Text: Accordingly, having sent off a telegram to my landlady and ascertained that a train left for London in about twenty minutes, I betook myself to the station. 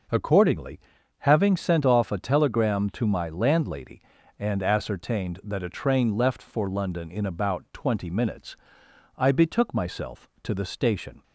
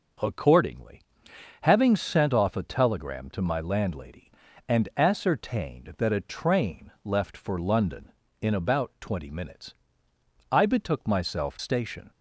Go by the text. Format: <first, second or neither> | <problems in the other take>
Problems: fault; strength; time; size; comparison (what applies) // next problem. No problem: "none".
first | skips "to the"; at 11.5 s